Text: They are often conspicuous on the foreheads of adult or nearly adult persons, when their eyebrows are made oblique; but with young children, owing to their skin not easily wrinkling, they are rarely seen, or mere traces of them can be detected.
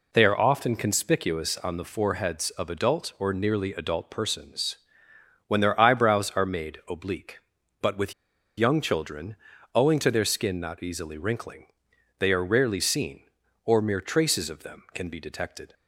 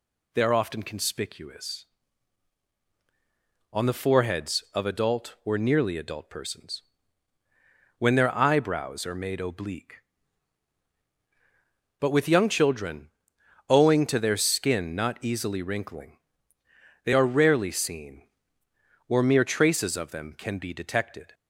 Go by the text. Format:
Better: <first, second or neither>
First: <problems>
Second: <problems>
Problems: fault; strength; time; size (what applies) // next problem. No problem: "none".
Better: second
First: pauses between "with" and "young"; at 8.1 s; 0.45 s long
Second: none